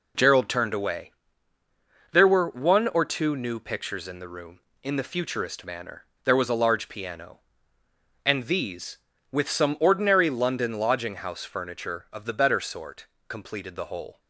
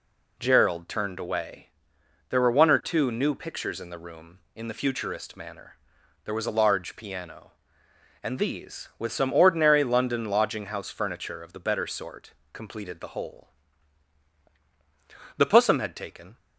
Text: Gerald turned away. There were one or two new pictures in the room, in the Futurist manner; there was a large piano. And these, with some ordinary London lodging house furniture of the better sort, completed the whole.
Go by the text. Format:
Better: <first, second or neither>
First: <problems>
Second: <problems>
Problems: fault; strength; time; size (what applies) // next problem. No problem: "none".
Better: first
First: none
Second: goes on to say "The Pussum had taken"; noticeable; from 15.3 s on; 1.0 s long